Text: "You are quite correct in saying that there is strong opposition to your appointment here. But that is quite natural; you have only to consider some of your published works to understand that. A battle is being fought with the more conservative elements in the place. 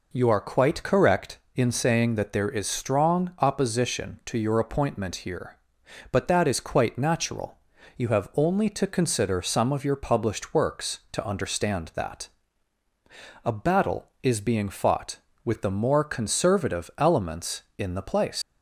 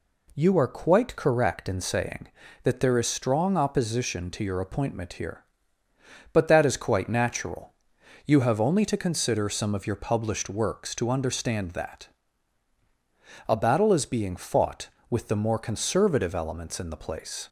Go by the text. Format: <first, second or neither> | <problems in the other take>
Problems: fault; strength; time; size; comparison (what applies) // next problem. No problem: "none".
second | leaves "place" unfinished; at 18.4 s; 105 ms